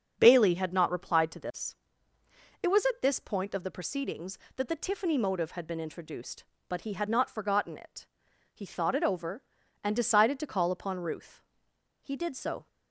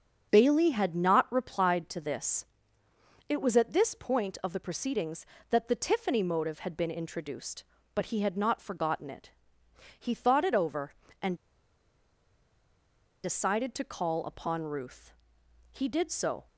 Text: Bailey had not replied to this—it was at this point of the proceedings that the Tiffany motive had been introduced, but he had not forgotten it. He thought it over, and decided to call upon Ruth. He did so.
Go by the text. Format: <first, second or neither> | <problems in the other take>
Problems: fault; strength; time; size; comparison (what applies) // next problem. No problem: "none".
first | starts louder than the rest; until 1.3 s; 7 dB; also in the first // pauses between "and" and "decided"; strong; at 11.3 s; 1.8 s long